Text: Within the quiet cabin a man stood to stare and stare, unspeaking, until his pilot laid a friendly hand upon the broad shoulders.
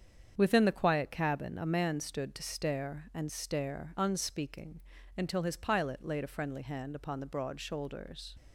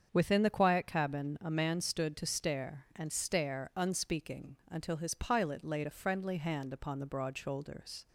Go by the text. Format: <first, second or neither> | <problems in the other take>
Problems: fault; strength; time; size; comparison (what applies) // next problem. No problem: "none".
neither | starts louder than the rest; strong; the same in both